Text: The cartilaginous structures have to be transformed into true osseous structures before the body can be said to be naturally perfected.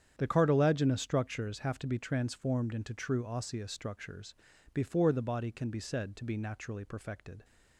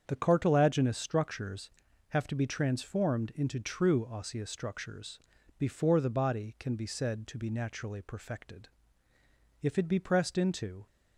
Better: first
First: starts louder than the rest; strong; until 1.1 s; 9 dB // pauses between "structures" and "before"; at 4.3 s; 0.40 s long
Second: starts louder than the rest; strong; until 1.0 s; 7.5 dB // pauses between "structures" and "before"; at 5.1 s; 0.40 s long // goes on to say "If it be pressed into"; noticeable; from 9.6 s on; 1.2 s long

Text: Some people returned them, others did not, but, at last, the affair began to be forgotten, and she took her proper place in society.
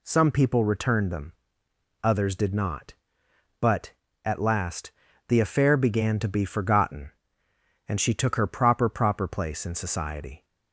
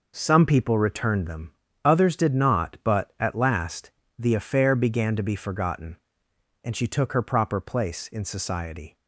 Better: second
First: says "proper" twice; at 8.8 s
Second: none

